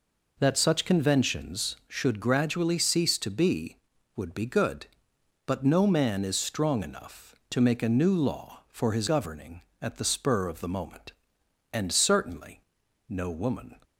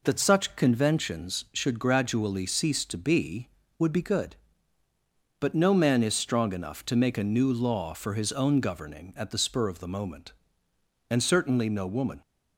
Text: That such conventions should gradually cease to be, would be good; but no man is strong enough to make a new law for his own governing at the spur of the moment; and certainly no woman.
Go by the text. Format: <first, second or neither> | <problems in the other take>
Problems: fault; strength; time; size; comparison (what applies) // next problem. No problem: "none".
second | skips "own"; at 9.0 s // pauses between "certainly" and "no"; noticeable; at 12.6 s; 0.48 s long